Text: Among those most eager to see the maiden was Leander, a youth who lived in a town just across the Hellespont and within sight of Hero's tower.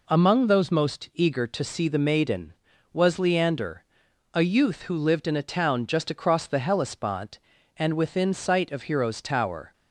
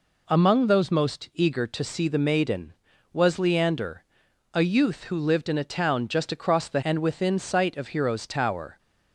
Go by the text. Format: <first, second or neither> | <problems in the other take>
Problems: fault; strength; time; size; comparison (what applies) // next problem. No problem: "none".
first | skips "Hellespont"; at 6.8 s